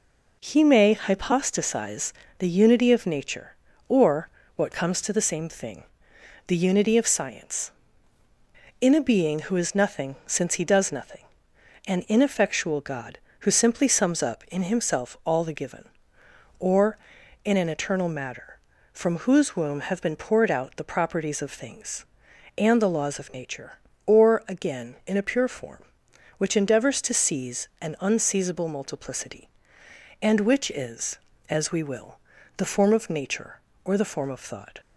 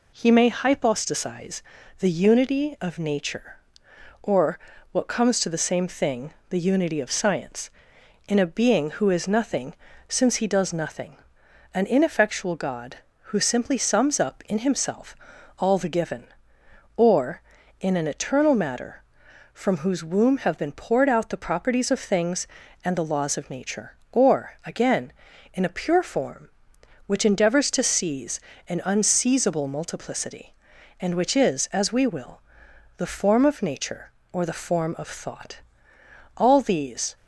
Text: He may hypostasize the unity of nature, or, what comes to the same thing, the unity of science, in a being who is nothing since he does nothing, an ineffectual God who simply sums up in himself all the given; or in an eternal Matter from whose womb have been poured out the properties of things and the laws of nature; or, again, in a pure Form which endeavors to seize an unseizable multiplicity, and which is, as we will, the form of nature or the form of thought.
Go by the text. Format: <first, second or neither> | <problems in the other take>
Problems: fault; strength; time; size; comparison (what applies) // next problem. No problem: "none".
first | pauses between "hypostasize" and "the"; slight; at 1.6 s; 0.36 s long; slight in the first // pauses between "nothing" and "since"; slight; at 9.7 s; 0.34 s long // pauses between "himself" and "all"; at 15.1 s; 0.42 s long // pauses between "seize" and "an"; slight; at 28.3 s; 0.30 s long // goes on to say "All these"; noticeable; from 36.3 s on; 0.78 s long